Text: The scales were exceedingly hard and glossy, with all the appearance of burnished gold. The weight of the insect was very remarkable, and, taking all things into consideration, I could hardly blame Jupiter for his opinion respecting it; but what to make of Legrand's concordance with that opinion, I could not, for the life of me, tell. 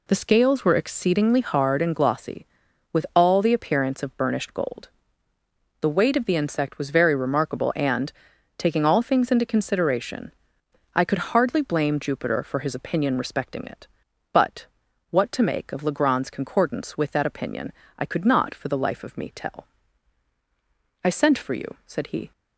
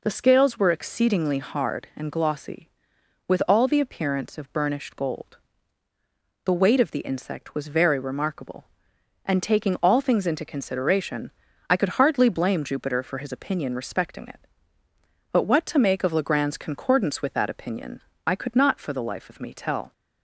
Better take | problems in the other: second | pauses between "but" and "what"; at 14.6 s; 0.44 s long // goes on to say "I sent for you said he"; noticeable; from 21.0 s on; 1.2 s long

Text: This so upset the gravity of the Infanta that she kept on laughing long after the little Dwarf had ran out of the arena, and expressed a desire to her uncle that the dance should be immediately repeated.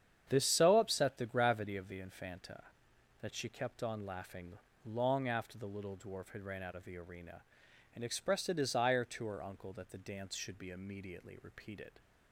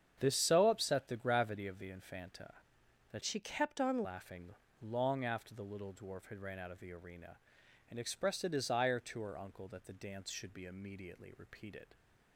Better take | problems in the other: first | starts louder than the rest; strong; until 1.2 s; 8 dB; strong in the first // changes voice from "she" to "on"; from 3.2 to 4.0 s; 0.8 s long // pauses between "laughing" and "long"; slight; at 4.5 s; 0.28 s long; slight in the first

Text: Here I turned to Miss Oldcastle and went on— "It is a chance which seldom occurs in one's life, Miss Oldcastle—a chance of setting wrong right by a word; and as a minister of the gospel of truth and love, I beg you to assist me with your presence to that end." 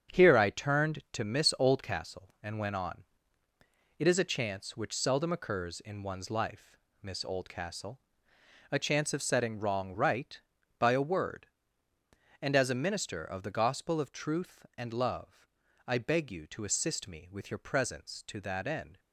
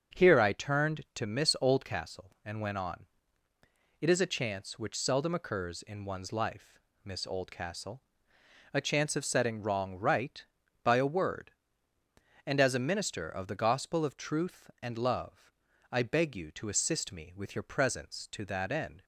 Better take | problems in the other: second | gets quieter; strong; throughout; 7.5 dB // starts louder than the rest; strong; until 1.2 s; 8 dB; also in the second

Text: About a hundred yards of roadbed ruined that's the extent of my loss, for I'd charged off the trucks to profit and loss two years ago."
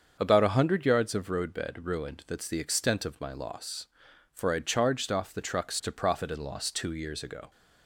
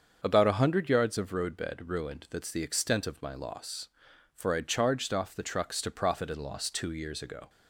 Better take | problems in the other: neither | starts louder than the rest; the same in both

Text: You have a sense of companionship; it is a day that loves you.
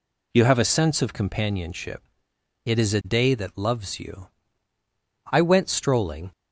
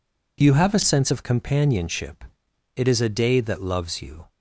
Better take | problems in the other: second | goes on to say "I went strolling"; noticeable; from 5.3 s on; 1.0 s long

